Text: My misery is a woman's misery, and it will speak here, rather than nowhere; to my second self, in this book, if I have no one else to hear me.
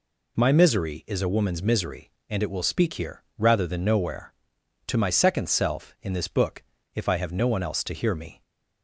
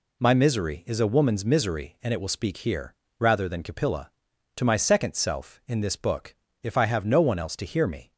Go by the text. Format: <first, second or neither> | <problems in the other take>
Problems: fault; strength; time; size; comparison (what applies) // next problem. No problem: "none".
first | says "capilla" for "nowhere"; at 3.6 s